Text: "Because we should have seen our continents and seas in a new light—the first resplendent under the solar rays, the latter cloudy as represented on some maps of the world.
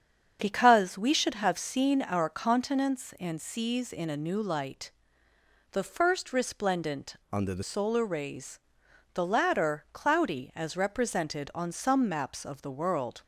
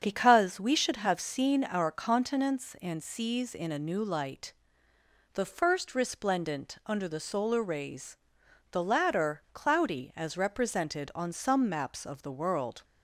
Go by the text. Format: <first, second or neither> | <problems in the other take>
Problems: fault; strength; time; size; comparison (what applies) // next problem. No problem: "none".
second | starts louder than the rest; strong; until 1.4 s; 7.5 dB; strong in the second // changes voice from "under" to "the"; from 7.3 to 7.6 s; 0.3 s long